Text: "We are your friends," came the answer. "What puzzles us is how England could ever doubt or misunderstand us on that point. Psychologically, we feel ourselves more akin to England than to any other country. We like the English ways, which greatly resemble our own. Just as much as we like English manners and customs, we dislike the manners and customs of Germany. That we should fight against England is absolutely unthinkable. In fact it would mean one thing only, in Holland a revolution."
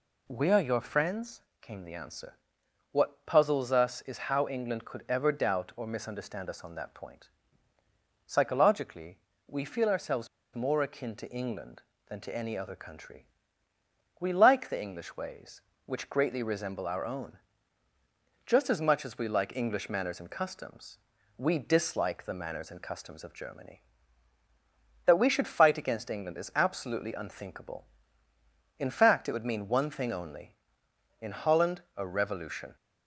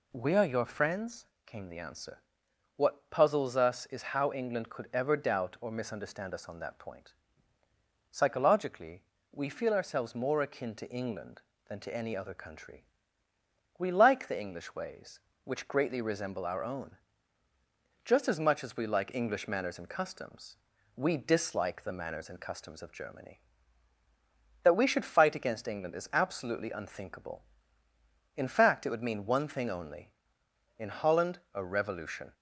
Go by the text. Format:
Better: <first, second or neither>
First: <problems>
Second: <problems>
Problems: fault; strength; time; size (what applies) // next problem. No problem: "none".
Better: second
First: pauses between "ourselves" and "more"; slight; at 10.2 s; 0.27 s long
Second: none